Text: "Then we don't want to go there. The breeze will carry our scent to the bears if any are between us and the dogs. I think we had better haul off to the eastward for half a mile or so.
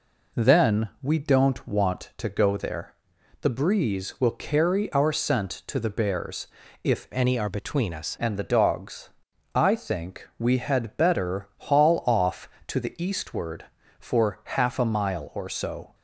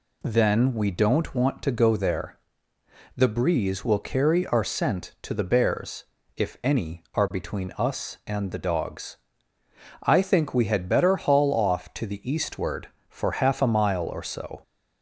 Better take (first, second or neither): second